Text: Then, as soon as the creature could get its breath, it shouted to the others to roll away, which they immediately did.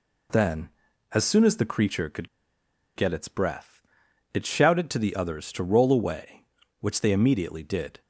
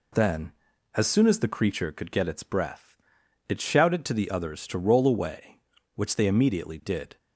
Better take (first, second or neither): second